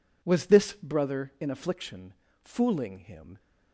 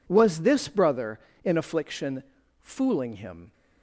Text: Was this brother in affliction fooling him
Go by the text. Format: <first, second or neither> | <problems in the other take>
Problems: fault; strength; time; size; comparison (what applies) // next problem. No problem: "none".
neither | pauses between "affliction" and "fooling"; the same in both